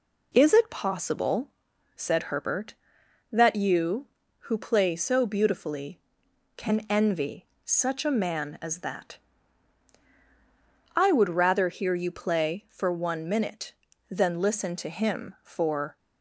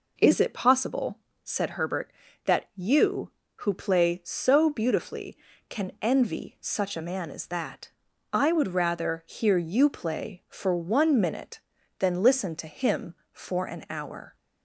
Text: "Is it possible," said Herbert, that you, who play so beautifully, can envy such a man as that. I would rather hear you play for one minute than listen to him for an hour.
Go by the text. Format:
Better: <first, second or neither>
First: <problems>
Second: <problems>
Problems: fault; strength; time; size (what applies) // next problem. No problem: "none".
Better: second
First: pauses between "envy" and "such"; slight; at 7.4 s; 0.18 s long // stops before "an hour"; at 15.9 s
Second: none